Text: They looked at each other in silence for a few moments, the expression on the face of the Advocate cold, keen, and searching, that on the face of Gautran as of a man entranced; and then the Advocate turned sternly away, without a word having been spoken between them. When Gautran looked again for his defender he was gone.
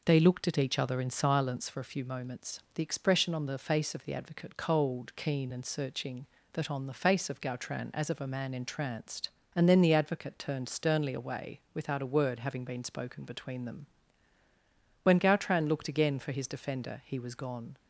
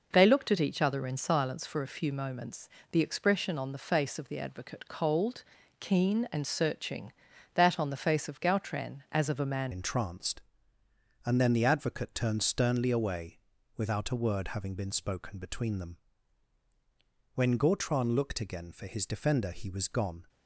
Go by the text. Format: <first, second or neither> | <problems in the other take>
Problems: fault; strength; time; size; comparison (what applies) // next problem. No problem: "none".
first | changes voice at "entranced"; from 9.7 s on; 10.5 s long